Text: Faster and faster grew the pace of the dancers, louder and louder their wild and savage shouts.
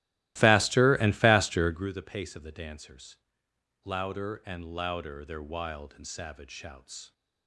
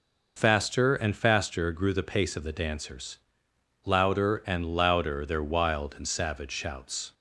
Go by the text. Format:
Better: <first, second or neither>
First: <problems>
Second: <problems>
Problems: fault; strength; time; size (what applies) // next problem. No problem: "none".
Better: second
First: starts louder than the rest; strong; until 1.9 s; 16.5 dB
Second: none